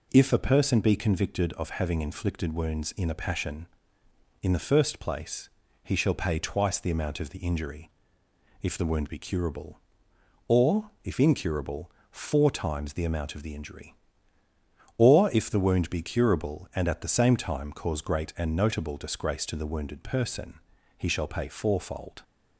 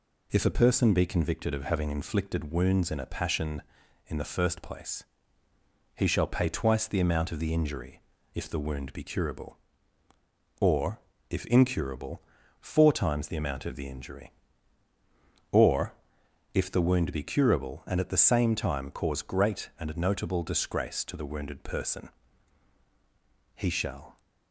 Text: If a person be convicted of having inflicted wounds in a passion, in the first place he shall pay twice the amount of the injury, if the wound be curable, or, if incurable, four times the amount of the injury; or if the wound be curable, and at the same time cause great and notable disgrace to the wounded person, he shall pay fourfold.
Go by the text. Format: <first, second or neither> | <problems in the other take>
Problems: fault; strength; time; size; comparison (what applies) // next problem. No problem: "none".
first | pauses between "place" and "he"; noticeable; at 5.0 s; 0.90 s long; slight in the first // pauses between "or" and "if"; noticeable; at 15.9 s; 0.60 s long // stops before "pay fourfold"; at 24.1 s